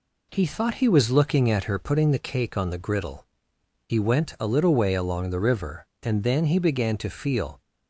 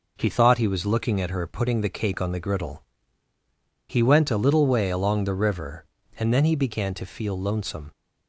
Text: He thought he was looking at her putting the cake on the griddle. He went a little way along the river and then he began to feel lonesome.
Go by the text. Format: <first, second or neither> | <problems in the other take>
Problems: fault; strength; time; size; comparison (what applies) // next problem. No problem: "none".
second | stops before "lonesome"; at 7.6 s